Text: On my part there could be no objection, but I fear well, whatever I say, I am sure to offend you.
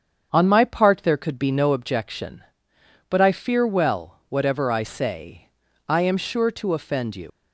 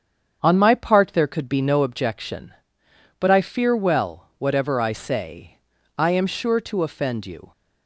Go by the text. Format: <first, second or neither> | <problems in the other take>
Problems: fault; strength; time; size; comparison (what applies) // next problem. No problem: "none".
second | starts louder than the rest; strong; until 1.3 s; 7.5 dB; strong in the second // leaves "you" unfinished; at 7.2 s; 110 ms